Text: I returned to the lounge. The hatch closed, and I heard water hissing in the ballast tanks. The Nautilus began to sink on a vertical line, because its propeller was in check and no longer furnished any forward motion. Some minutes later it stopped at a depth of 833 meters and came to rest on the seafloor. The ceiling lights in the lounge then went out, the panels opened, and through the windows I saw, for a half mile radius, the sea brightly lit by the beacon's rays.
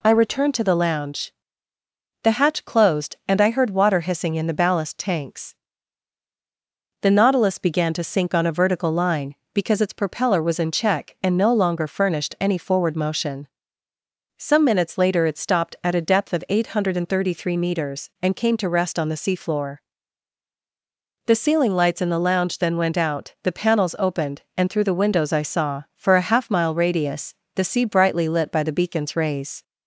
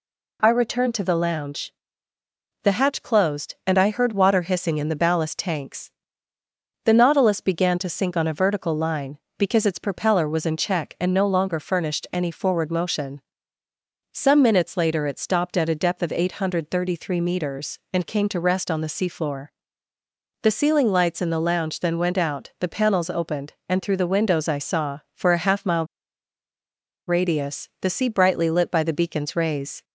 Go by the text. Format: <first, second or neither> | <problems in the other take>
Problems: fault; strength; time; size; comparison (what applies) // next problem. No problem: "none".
first | pauses between "mile" and "radius"; at 25.8 s; 1.2 s long